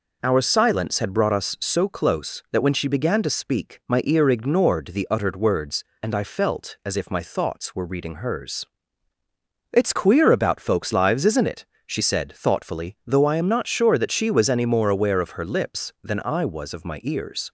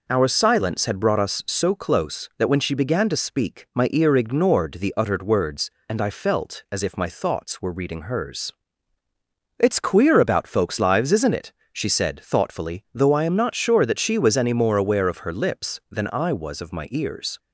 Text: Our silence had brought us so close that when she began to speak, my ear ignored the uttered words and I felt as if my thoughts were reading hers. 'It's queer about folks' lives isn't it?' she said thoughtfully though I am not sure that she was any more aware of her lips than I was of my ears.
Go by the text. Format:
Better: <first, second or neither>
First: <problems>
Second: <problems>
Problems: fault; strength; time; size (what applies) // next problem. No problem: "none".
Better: neither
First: none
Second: none